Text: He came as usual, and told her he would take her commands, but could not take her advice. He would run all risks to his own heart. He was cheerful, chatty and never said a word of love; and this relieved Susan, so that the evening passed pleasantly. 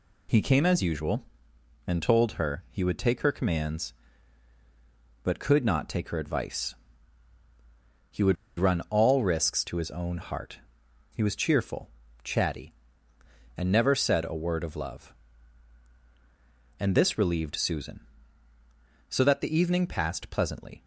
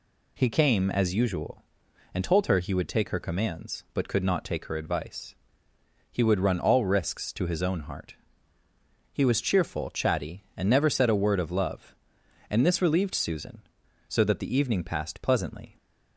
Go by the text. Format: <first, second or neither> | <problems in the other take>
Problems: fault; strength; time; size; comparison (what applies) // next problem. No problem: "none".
second | pauses between "would" and "run"; slight; at 8.3 s; 0.23 s long